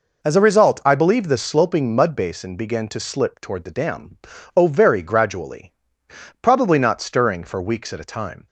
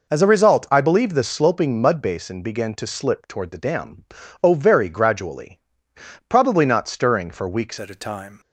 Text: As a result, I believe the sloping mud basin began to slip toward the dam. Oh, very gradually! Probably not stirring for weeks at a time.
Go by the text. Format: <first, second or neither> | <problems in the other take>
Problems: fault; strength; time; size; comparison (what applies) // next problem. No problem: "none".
first | changes voice at "at"; from 7.7 s on; 0.6 s long